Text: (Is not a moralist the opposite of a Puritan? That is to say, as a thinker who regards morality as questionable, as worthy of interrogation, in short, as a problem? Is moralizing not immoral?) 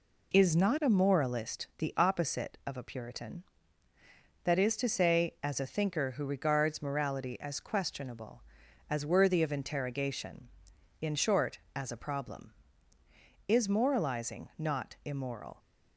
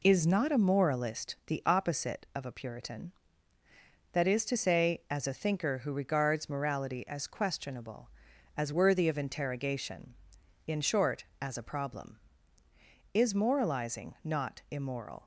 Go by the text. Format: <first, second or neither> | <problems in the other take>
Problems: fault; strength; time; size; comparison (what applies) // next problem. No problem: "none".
neither | none